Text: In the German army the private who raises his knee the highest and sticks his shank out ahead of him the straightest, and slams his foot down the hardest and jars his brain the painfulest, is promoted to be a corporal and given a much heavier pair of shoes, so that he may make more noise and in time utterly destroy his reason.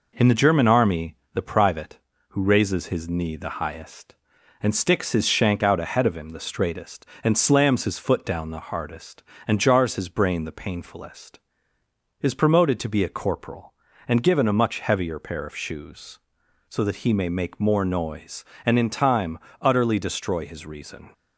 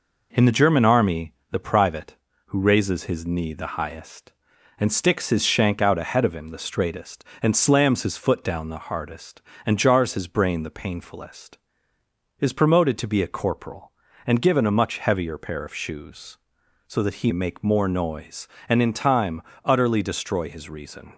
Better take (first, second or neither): first